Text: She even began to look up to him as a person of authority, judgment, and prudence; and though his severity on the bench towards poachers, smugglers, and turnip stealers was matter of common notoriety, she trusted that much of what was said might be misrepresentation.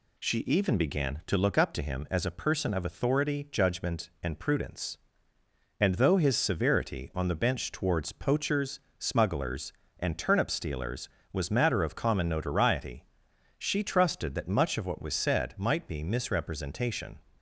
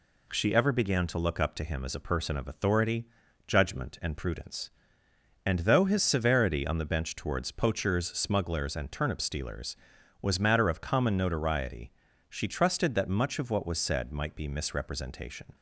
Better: first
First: none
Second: says "ever" for "even"; at 0.5 s

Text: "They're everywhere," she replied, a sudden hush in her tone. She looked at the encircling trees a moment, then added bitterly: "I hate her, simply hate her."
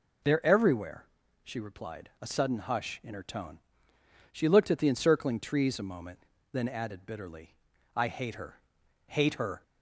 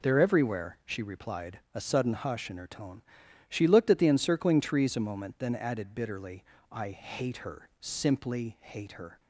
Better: second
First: skips "simply"; at 8.8 s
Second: none

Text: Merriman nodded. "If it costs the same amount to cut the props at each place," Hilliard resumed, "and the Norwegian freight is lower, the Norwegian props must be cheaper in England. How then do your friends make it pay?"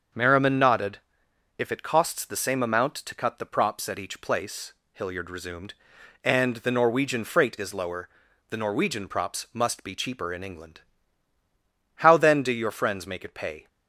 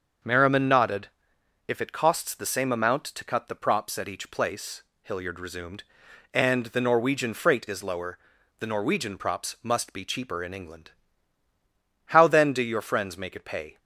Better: neither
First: starts louder than the rest; until 1.7 s; 6.5 dB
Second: starts louder than the rest; until 1.8 s; 6.5 dB

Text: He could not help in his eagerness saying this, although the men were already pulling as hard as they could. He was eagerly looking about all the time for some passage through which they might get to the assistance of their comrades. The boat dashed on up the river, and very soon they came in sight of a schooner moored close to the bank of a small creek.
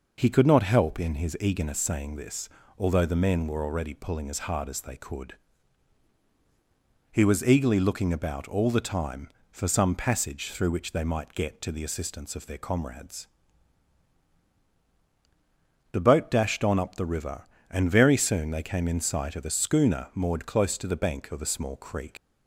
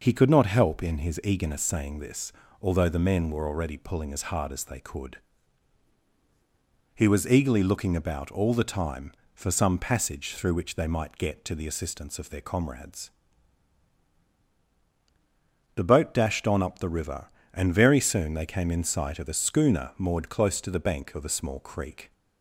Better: second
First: leaves "creek" unfinished; at 22.1 s; 120 ms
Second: none

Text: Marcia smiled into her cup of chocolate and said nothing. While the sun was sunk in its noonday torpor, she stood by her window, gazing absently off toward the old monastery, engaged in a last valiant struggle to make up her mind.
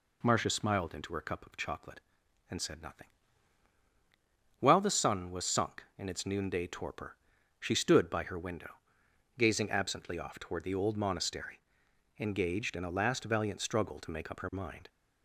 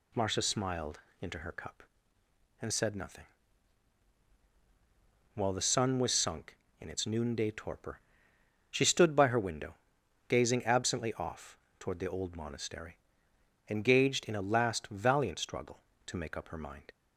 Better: first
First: none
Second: pauses between "smiled" and "into"; slight; at 1.0 s; 0.20 s long // skips "of chocolate"; at 2.2 s // pauses between "off" and "toward"; slight; at 11.5 s; 0.22 s long

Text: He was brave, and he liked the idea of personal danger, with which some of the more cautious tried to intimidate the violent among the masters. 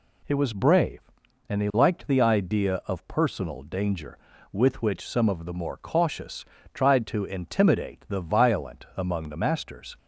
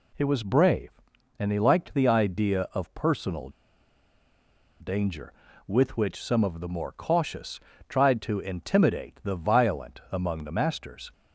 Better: first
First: pauses between "cautious" and "tried"; slight; at 6.4 s; 0.30 s long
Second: pauses between "personal" and "danger"; strong; at 3.4 s; 1.3 s long // pauses between "cautious" and "tried"; slight; at 7.5 s; 0.30 s long

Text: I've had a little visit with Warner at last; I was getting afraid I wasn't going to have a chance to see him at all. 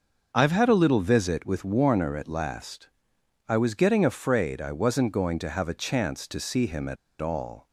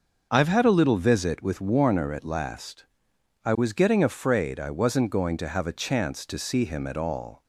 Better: second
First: starts louder than the rest; until 1.3 s; 6 dB // pauses between "at" and "all"; slight; at 6.9 s; 0.24 s long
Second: starts louder than the rest; until 1.3 s; 6.5 dB

